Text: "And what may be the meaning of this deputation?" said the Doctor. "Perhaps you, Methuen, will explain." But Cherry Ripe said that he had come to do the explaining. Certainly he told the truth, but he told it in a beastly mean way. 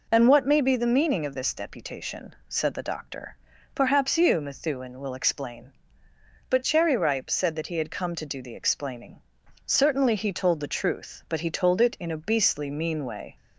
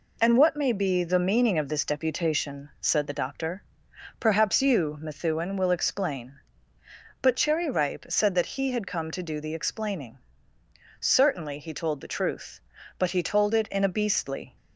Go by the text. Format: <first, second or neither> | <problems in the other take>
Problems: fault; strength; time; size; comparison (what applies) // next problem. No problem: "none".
first | stops before "mean way"; at 14.5 s